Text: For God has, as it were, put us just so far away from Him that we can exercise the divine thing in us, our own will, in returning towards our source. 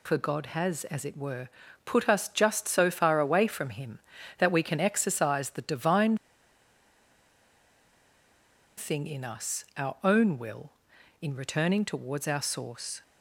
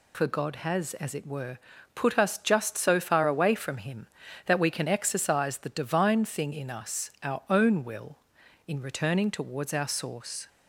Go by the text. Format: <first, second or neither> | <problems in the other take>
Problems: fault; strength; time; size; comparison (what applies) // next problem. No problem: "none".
second | pauses between "divine" and "thing"; strong; at 6.1 s; 2.6 s long